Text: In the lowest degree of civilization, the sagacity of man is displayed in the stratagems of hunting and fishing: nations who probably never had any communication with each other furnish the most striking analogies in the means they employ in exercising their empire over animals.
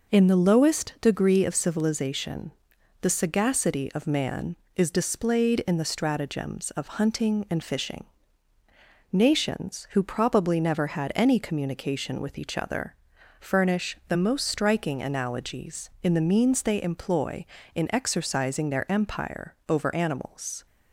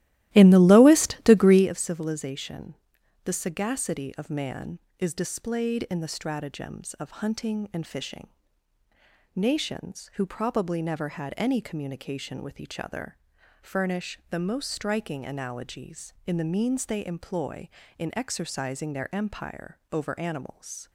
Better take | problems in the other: first | starts louder than the rest; strong; until 1.7 s; 15.5 dB // pauses between "other" and "furnish"; at 13.1 s; 0.44 s long; also in the first

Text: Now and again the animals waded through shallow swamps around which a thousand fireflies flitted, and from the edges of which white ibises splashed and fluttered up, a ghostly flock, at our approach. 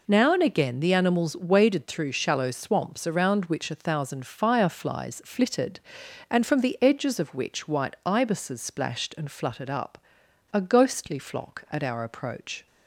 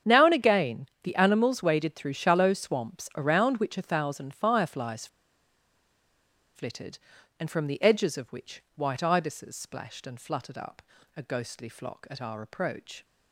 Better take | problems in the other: first | starts louder than the rest; strong; until 1.2 s; 8 dB // pauses between "again" and "the"; slight; at 0.8 s; 0.16 s long // pauses between "fireflies" and "flitted"; strong; at 5.0 s; 1.4 s long

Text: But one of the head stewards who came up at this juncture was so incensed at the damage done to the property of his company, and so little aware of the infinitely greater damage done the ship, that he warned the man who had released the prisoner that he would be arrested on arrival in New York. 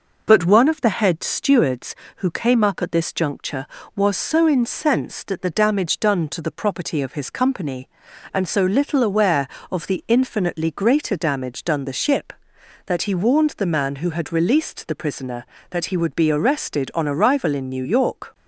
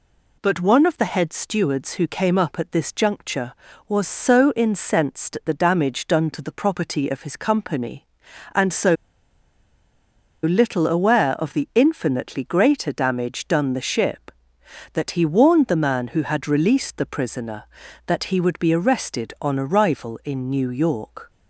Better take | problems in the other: first | pauses between "so" and "little"; strong; at 8.9 s; 1.4 s long

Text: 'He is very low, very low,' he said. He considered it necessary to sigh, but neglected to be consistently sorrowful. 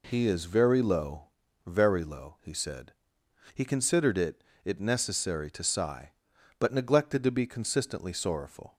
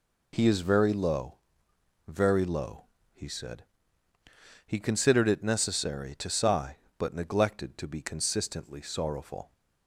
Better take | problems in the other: second | says "it" twice; at 4.6 s

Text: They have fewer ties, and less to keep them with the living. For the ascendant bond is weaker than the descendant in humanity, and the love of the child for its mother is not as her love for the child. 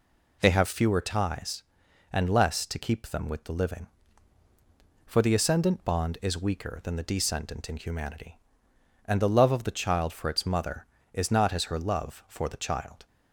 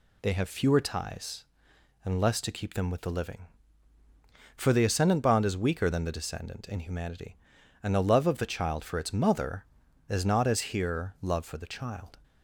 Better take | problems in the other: first | says "here" for "her"; at 10.7 s

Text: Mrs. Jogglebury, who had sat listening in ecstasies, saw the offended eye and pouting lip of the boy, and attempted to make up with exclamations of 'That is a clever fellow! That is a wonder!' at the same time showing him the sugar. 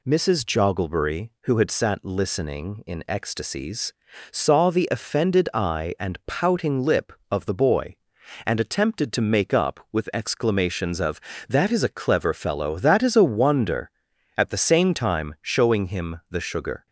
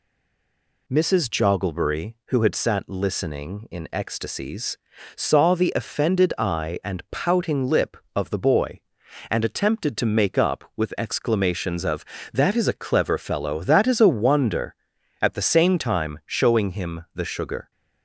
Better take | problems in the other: first | stays silent before the first word; slight; until 0.8 s; 0.8 s long

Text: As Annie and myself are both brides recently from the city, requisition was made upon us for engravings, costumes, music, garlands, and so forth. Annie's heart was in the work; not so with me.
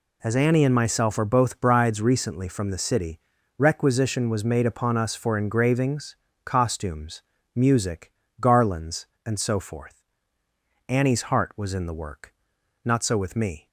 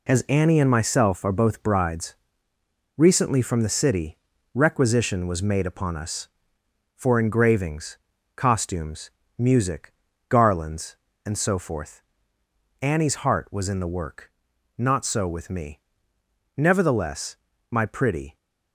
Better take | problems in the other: first | pauses between "brides" and "recently"; noticeable; at 2.1 s; 0.80 s long // goes on to say "Nevertheless my pretty"; strong; from 16.5 s on; 1.8 s long

